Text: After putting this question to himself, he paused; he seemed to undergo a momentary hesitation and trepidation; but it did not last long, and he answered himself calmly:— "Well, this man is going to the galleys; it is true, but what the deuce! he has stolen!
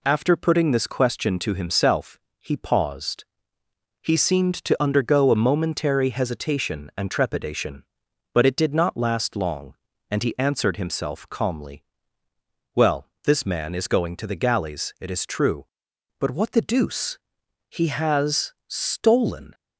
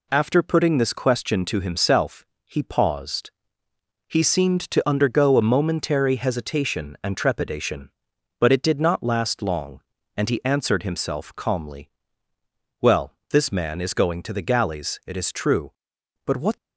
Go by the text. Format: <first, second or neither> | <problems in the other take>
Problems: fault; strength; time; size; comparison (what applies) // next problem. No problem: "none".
first | stops before "the deuce he has stolen"; at 16.5 s